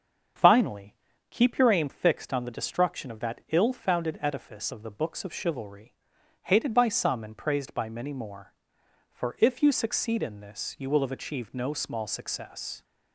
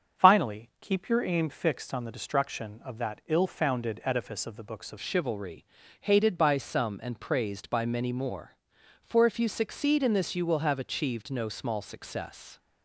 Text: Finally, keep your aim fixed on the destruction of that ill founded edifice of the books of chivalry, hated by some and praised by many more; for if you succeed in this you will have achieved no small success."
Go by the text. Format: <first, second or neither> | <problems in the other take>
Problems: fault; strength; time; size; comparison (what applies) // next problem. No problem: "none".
first | starts louder than the rest; until 1.3 s; 7 dB; strong in the first // changes voice at "chivalry"; from 5.0 s on; 7.5 s long